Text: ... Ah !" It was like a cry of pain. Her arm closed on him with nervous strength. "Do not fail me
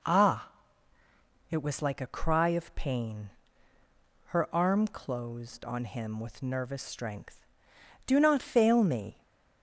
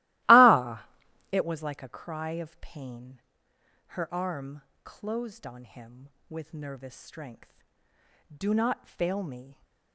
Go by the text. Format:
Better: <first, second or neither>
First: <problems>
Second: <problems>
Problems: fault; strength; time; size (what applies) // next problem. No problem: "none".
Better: first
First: none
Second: starts louder than the rest; strong; until 1.4 s; 17 dB // pauses between "arm" and "closed"; slight; at 4.6 s; 0.24 s long